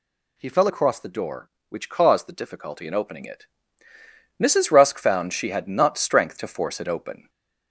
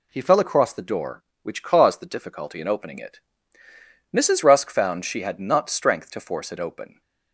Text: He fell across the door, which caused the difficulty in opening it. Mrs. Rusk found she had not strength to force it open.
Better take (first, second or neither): second